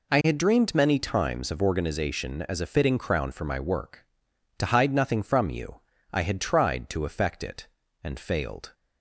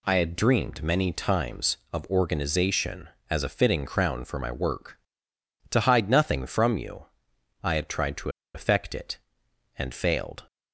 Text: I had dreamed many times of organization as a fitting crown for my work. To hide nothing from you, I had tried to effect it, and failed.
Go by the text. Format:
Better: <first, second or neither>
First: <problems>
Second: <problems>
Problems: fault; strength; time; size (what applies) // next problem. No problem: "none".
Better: first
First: none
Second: pauses between "to" and "effect"; slight; at 8.2 s; 0.25 s long